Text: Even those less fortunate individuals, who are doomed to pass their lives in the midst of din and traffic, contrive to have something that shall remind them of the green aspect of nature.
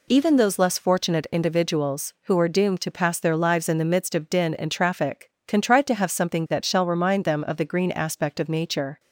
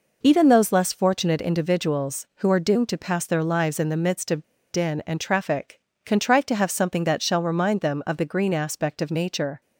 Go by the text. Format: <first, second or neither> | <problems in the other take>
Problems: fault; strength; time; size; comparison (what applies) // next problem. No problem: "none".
first | pauses between "of" and "din"; slight; at 4.4 s; 0.27 s long